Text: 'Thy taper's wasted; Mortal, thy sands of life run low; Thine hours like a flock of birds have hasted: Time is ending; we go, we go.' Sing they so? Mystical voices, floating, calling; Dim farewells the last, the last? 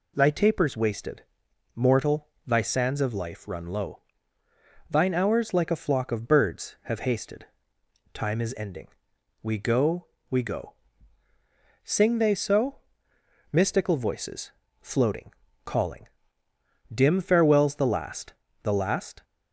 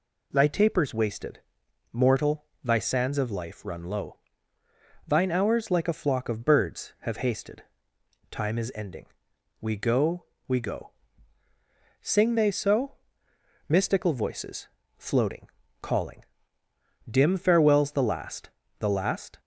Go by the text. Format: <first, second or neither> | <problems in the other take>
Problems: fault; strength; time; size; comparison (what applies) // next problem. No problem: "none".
neither | none